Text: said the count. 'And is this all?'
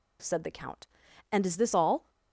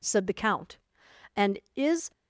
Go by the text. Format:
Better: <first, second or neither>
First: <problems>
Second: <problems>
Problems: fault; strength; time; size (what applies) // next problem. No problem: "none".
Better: first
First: none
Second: stops before "this all"; at 2.1 s